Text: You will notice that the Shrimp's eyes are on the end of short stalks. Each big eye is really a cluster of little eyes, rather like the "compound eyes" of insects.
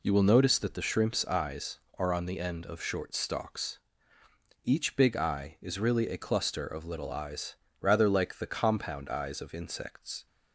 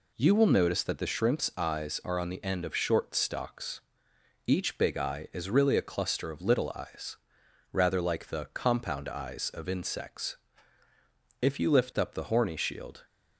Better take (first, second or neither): first